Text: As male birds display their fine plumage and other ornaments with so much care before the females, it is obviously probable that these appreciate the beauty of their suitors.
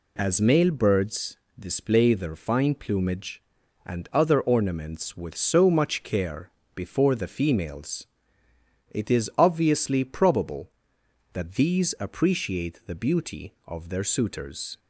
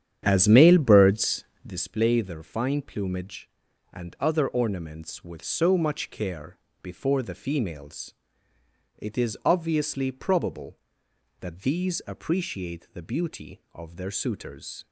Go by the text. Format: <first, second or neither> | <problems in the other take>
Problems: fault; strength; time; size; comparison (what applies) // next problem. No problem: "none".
first | starts louder than the rest; strong; until 1.9 s; 9.5 dB // pauses between "birds" and "display"; slight; at 1.4 s; 0.22 s long; slight in the first // pauses between "care" and "before"; slight; at 6.5 s; 0.26 s long; slight in the first